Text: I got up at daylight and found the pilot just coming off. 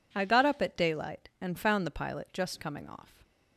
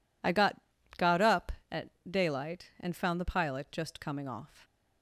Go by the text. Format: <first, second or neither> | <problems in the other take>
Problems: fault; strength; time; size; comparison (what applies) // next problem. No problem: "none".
first | says "got" twice; at 0.9 s // pauses between "at" and "daylight"; slight; at 1.8 s; 0.20 s long